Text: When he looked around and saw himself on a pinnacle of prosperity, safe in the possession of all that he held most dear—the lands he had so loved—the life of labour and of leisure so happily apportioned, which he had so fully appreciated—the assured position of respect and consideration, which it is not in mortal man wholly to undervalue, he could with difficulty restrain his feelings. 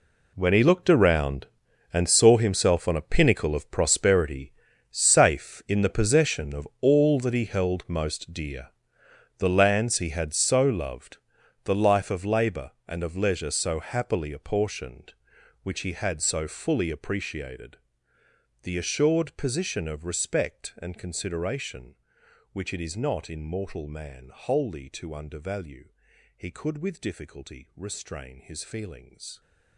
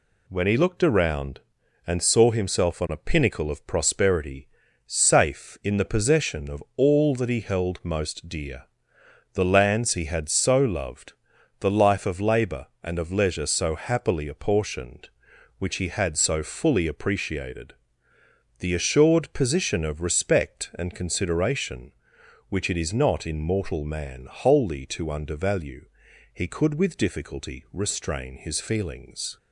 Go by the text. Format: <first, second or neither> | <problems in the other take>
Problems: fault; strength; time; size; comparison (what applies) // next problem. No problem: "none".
second | gets quieter; strong; throughout; 14.5 dB